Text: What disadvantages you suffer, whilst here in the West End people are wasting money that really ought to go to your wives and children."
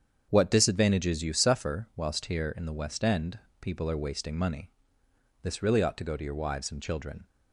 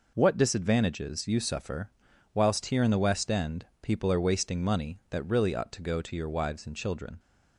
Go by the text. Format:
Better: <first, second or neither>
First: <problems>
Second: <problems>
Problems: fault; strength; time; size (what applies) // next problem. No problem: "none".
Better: second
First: starts louder than the rest; strong; until 1.3 s; 7.5 dB // pauses between "End" and "people"; slight; at 3.3 s; 0.22 s long // says "this" for "that"; at 5.4 s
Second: pauses between "End" and "people"; slight; at 3.6 s; 0.16 s long